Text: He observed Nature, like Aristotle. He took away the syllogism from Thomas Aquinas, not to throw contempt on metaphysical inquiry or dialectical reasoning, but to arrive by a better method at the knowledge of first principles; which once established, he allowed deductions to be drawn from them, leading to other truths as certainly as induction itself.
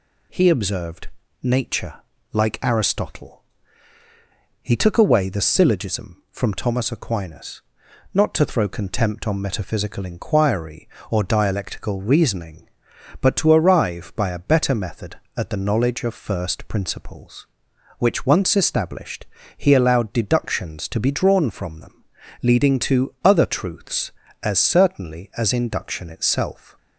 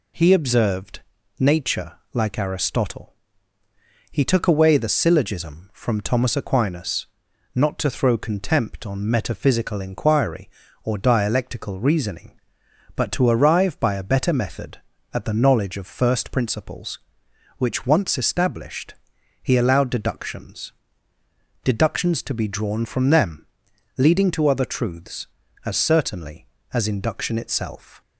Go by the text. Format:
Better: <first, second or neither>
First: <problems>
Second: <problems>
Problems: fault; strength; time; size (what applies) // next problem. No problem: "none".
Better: first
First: pauses between "observed" and "Nature"; slight; at 1.0 s; 0.34 s long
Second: pauses between "observed" and "Nature"; at 1.0 s; 0.40 s long // says "deductions" twice; at 21.6 s